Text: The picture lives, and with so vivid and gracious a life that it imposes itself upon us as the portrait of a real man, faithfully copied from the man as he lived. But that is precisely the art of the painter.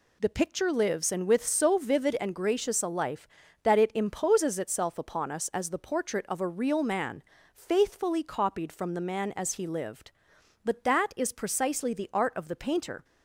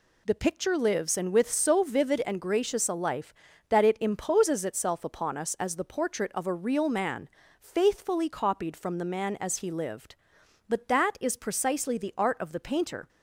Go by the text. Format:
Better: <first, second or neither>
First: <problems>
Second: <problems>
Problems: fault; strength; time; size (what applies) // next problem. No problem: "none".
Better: neither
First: none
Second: none